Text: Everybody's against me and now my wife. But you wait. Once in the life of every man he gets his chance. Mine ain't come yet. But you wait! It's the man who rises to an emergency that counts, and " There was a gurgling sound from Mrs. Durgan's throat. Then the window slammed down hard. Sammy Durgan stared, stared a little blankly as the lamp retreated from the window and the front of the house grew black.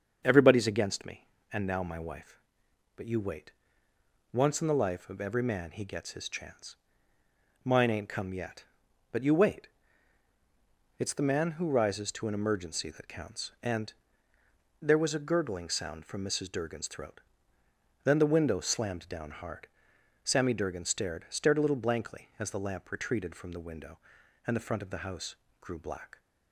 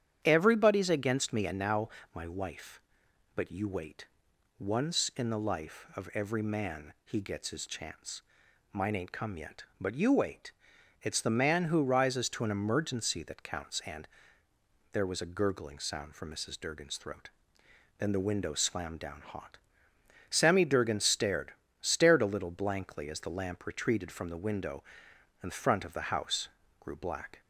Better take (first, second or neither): first